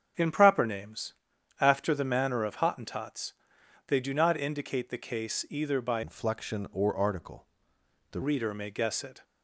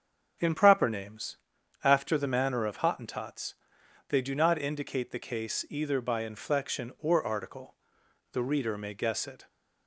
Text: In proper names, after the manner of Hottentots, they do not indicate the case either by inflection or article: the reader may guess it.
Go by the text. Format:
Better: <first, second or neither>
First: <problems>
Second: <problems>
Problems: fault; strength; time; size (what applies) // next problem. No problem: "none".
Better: second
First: starts louder than the rest; strong; until 1.6 s; 7.5 dB // changes voice from "inflection" to "the"; from 6.0 to 8.2 s; 2.2 s long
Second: starts louder than the rest; strong; until 1.8 s; 7.5 dB